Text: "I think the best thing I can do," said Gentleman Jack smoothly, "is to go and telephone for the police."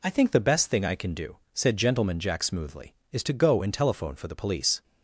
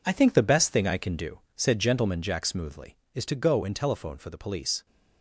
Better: first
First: none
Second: gets quieter; strong; throughout; 10.5 dB

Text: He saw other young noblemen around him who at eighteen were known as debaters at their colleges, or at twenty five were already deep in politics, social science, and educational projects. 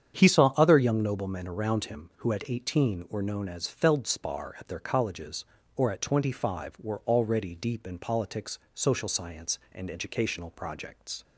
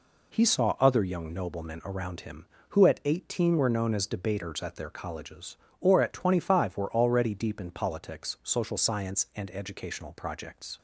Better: second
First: starts louder than the rest; strong; until 1.1 s; 8.5 dB // says "feldspar" for "debaters"; at 3.6 s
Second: none

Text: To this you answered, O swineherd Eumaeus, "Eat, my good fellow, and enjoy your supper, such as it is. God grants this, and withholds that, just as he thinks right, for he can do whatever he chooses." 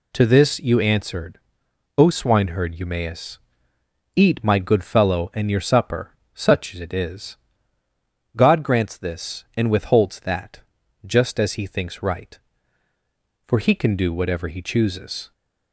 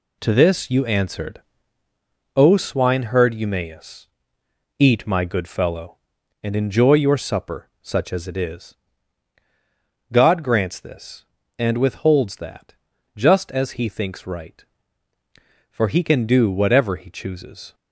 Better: second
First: skips "enjoy"; at 5.4 s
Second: none

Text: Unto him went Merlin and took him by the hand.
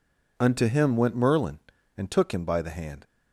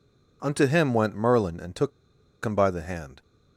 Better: first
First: none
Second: pauses between "took" and "him"; noticeable; at 1.9 s; 0.54 s long

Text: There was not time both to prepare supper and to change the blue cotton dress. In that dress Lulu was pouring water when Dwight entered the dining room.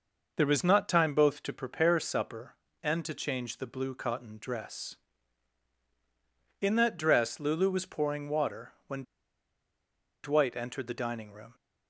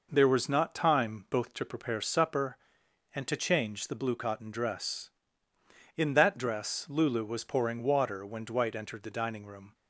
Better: second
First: pauses between "when" and "Dwight"; at 9.0 s; 1.2 s long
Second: none

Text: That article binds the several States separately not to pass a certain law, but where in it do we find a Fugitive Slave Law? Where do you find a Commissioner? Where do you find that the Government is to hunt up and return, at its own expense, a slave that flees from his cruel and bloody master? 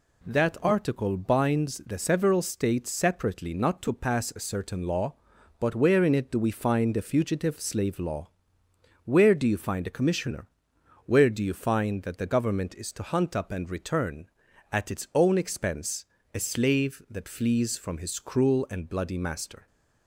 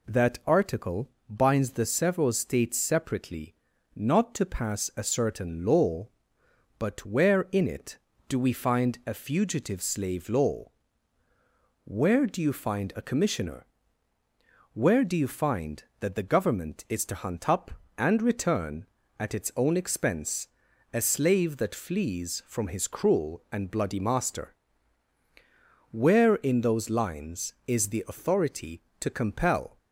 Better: first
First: none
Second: pauses between "article" and "binds"; slight; at 1.0 s; 0.20 s long // pauses between "separately" and "not"; at 3.5 s; 0.40 s long // goes on to say "Where in those lines is the authority to compel"; strong; from 25.9 s on; 3.8 s long

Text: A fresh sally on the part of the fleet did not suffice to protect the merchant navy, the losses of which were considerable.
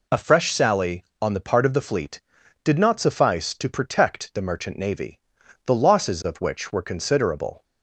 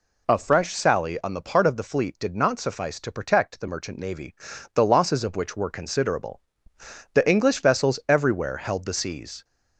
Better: first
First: none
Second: goes on to say "The English vessels everywhere held the seas"; strong; from 7.1 s on; 2.3 s long

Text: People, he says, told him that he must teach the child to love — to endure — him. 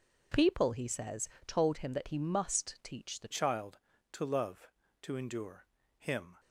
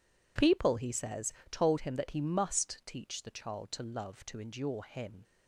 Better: second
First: changes voice at "child"; from 3.3 s on; 3.0 s long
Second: none

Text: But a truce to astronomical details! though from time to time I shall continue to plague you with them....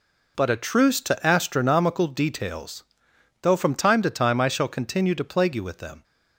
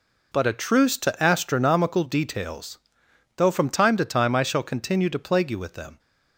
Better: neither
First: none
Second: none

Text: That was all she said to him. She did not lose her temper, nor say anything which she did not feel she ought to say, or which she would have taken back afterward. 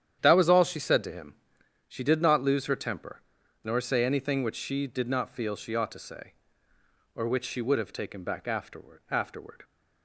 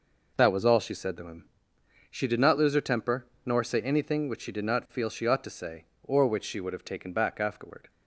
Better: second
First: starts louder than the rest; strong; until 1.2 s; 9.5 dB // says "afterward" twice; at 9.0 s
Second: none

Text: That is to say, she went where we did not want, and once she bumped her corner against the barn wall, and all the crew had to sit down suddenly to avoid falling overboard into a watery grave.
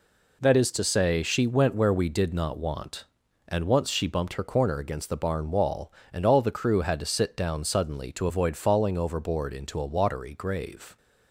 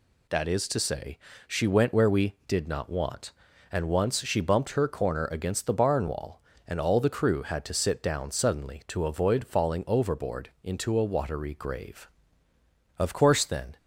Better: first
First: none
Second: goes on to say "Of course then"; noticeable; from 12.9 s on; 0.80 s long

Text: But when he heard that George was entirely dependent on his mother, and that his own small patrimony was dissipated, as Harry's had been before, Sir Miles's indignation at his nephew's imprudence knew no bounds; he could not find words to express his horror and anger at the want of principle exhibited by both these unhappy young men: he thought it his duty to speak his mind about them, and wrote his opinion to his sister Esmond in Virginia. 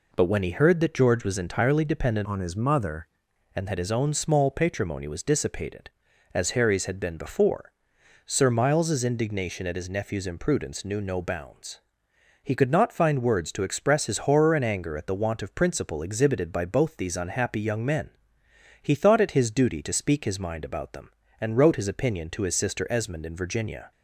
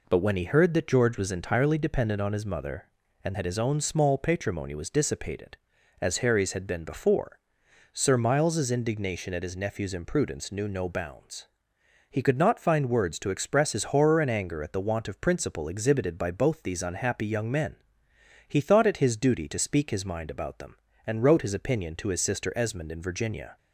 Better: second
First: changes voice from "on" to "mother"; from 2.2 to 3.0 s; 0.8 s long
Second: none

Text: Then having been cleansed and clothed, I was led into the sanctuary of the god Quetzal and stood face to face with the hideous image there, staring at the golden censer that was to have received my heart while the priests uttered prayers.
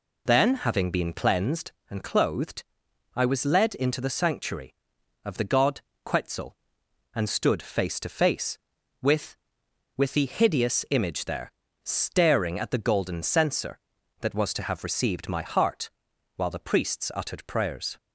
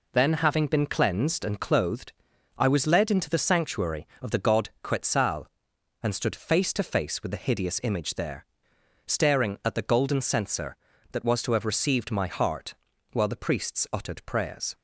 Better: second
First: pauses between "god" and "Quetzal"; slight; at 5.8 s; 0.24 s long // says "with" twice; at 9.9 s // pauses between "heart" and "while"; at 15.9 s; 0.44 s long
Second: pauses between "heart" and "while"; at 12.7 s; 0.38 s long

